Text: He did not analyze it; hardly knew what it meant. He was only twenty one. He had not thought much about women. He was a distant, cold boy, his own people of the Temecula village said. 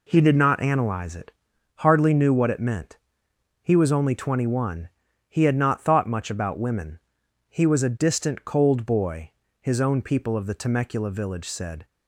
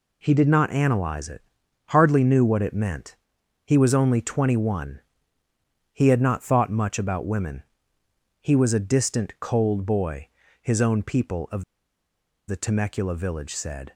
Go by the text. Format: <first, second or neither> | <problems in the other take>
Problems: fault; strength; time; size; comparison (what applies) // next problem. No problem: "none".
first | pauses between "of" and "the"; noticeable; at 11.6 s; 0.85 s long